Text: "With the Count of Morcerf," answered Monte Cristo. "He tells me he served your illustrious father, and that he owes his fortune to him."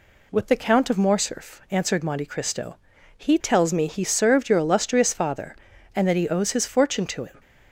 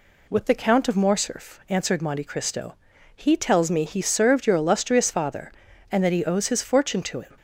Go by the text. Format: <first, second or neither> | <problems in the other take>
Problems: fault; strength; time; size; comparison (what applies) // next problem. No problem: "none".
neither | none